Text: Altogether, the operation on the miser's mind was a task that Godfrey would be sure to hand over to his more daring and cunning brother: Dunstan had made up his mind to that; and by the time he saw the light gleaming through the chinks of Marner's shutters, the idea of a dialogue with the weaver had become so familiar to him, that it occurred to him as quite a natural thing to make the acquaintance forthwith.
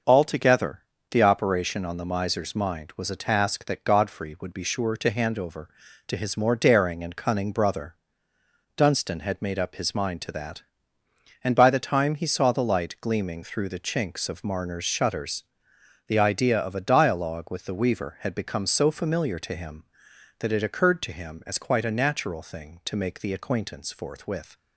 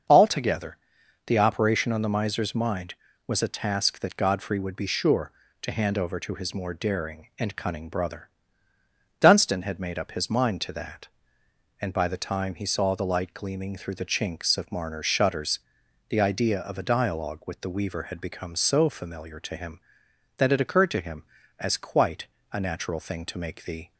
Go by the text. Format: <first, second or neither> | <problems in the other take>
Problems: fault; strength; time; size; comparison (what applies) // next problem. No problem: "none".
first | starts louder than the rest; until 1.5 s; 6.5 dB; also in the first // pauses between "quite" and "a"; slight; at 22.2 s; 0.26 s long // stops before "acquaintance forthwith"; at 23.9 s